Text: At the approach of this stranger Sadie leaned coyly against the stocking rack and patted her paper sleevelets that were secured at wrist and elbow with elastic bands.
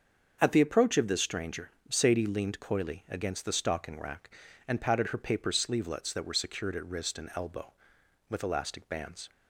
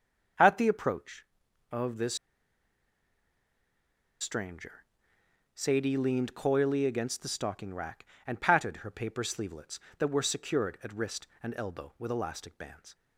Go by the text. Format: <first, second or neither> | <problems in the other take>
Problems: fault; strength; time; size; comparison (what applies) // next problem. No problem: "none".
first | starts louder than the rest; until 1.8 s; 6.5 dB; also in the first // pauses between "this" and "stranger"; strong; at 2.1 s; 2.0 s long // pauses between "stranger" and "Sadie"; noticeable; at 4.8 s; 0.70 s long; slight in the first